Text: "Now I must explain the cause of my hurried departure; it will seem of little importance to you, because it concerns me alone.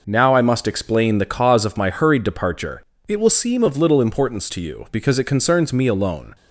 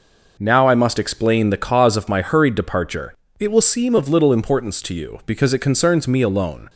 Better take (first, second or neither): neither